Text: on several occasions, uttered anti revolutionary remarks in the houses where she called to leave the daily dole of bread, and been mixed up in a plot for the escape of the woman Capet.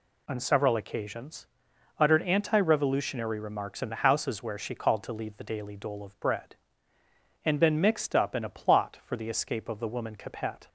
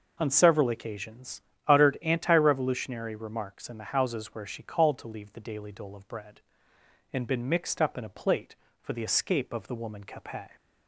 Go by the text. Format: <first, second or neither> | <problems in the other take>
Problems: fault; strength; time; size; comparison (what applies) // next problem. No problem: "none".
first | says "plate" for "plot"; at 8.0 s